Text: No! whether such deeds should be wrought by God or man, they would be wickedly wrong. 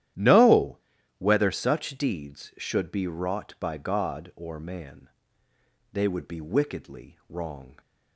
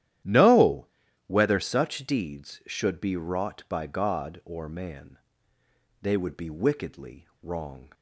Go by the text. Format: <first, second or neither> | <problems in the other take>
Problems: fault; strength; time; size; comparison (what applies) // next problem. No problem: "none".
neither | starts louder than the rest; strong; the same in both